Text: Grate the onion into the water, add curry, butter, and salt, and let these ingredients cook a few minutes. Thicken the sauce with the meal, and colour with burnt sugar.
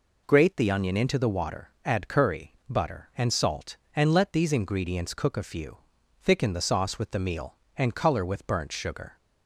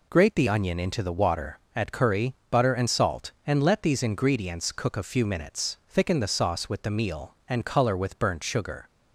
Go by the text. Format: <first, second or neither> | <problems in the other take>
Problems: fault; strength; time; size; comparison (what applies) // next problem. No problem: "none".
second | skips "minutes"; at 5.9 s